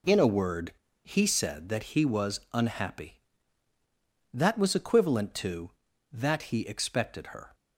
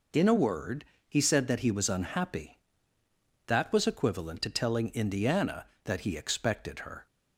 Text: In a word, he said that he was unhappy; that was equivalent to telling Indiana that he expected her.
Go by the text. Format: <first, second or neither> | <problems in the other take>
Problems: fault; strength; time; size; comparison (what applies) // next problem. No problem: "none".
second | skips "telling Indiana"; at 5.9 s